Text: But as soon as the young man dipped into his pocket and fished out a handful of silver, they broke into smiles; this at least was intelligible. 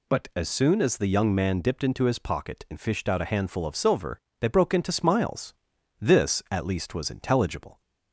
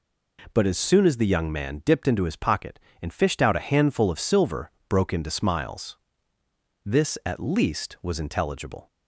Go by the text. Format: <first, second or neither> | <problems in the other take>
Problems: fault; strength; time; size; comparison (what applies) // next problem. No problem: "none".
first | skips "they"; at 4.7 s